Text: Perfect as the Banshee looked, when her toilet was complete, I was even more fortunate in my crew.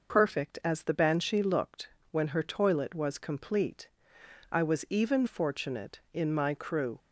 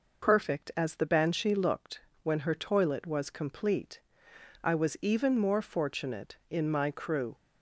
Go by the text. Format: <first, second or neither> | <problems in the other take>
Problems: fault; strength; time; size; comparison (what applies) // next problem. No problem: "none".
second | skips "more"; at 5.2 s